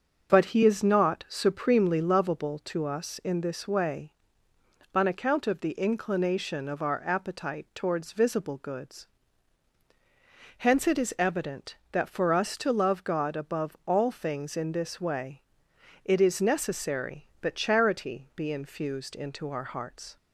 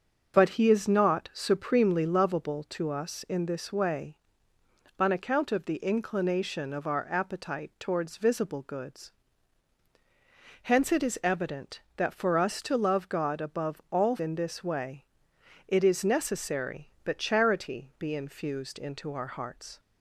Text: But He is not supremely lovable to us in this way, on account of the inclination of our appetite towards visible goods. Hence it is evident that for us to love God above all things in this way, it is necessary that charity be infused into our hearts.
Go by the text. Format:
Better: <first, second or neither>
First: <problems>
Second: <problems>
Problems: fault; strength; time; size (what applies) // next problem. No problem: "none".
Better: first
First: starts louder than the rest; noticeable; until 1.3 s; 6 dB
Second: starts louder than the rest; until 1.3 s; 6.5 dB // skips "things"; at 14.1 s